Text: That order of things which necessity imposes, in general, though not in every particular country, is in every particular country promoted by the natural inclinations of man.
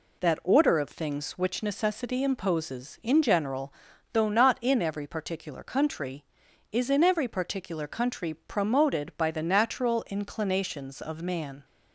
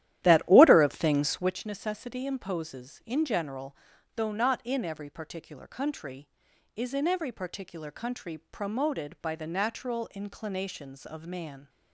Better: first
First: none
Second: starts louder than the rest; strong; until 1.6 s; 12.5 dB

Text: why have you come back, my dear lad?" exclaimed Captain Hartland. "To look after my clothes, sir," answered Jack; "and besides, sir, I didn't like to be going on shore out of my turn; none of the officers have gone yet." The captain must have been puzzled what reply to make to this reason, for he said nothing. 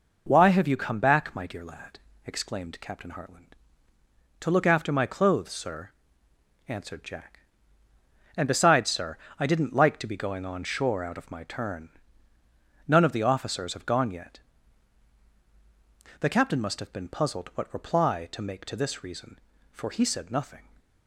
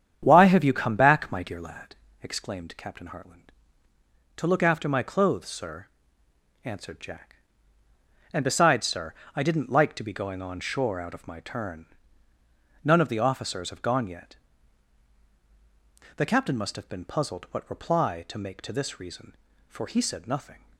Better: first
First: none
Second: starts louder than the rest; strong; until 1.9 s; 8.5 dB

